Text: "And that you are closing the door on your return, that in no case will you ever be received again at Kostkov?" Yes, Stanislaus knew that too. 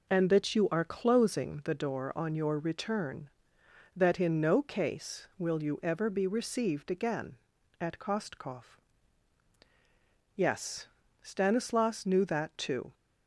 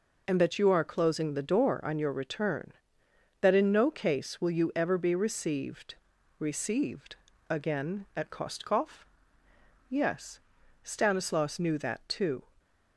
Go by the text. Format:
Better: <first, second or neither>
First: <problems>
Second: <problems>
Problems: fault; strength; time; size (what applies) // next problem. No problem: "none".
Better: first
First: none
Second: says "received" twice; at 6.3 s